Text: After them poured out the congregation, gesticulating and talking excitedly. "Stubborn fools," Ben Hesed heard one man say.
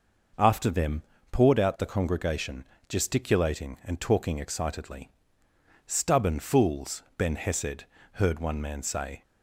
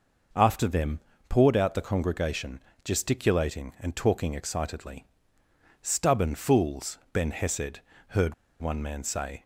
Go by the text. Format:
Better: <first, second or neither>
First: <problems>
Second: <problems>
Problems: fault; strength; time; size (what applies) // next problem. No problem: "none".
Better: first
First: pauses between "them" and "poured"; slight; at 1.0 s; 0.28 s long // pauses between "Hesed" and "heard"; slight; at 7.8 s; 0.28 s long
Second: pauses between "them" and "poured"; slight; at 0.9 s; 0.28 s long // pauses between "Hesed" and "heard"; slight; at 7.7 s; 0.28 s long // pauses between "heard" and "one"; slight; at 8.3 s; 0.25 s long